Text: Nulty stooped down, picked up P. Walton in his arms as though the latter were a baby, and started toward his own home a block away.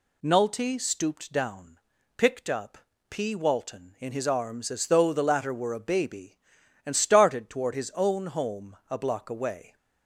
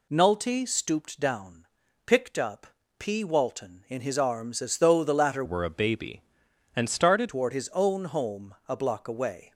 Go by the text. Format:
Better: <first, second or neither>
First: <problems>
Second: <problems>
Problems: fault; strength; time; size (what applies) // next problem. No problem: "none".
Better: first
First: pauses between "up" and "P"; slight; at 2.7 s; 0.32 s long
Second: pauses between "up" and "P"; slight; at 2.6 s; 0.32 s long // changes voice from "were" to "started"; from 5.4 to 7.2 s; 1.8 s long